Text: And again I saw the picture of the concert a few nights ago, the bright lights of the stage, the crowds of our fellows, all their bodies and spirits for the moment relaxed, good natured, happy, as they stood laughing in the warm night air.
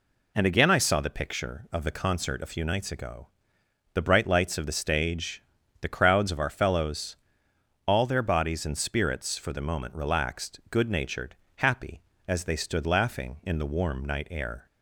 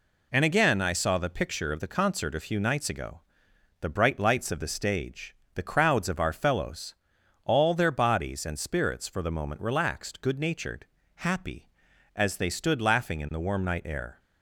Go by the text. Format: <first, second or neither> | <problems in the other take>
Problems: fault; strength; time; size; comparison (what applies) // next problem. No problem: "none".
neither | none